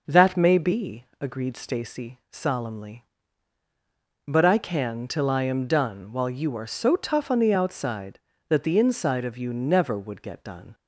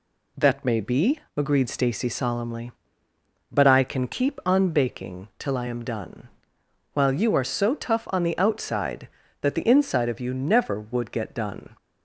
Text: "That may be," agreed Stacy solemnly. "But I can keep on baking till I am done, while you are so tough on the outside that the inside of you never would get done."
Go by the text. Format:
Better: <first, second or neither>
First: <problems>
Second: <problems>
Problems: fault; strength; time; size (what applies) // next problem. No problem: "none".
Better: second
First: skips "keep on baking"; at 5.0 s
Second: none